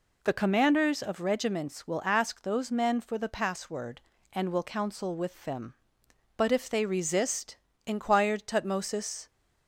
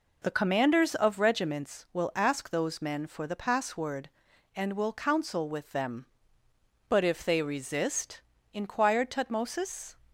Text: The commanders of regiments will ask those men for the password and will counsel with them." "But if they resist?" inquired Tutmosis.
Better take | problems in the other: neither | none

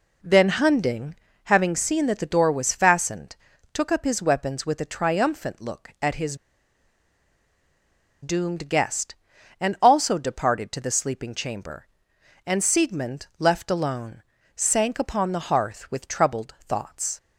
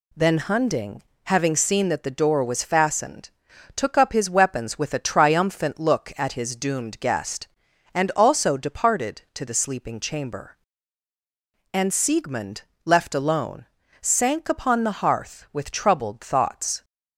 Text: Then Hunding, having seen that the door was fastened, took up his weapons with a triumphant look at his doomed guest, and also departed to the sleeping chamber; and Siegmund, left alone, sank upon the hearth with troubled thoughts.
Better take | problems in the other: second | pauses between "his" and "doomed"; strong; at 6.3 s; 1.8 s long

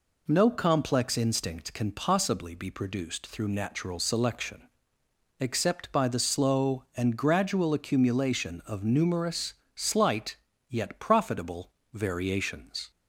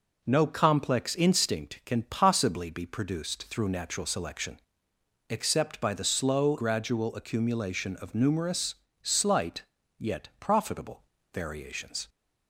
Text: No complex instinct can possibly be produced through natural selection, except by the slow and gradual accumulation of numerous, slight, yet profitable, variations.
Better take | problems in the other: first | skips "and"; at 6.5 s

